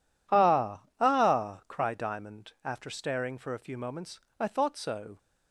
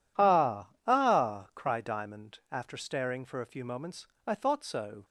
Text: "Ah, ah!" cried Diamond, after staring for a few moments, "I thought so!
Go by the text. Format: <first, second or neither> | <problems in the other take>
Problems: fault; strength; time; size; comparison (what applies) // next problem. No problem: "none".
neither | none